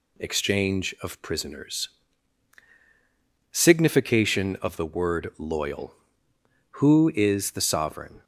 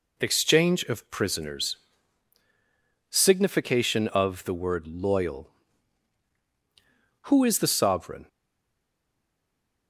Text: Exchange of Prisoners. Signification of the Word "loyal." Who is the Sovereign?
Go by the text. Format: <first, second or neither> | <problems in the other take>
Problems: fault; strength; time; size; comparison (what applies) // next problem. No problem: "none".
first | stays silent after the last word; noticeable; from 8.2 s on; 1.6 s long